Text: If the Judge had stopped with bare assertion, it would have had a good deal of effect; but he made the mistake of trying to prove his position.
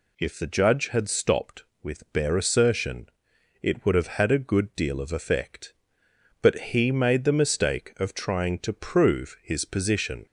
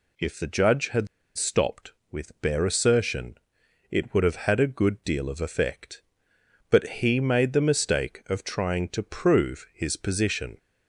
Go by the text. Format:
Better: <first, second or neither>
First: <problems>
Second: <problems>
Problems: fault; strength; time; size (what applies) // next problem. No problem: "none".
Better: first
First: none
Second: pauses between "had" and "stopped"; slight; at 1.0 s; 0.30 s long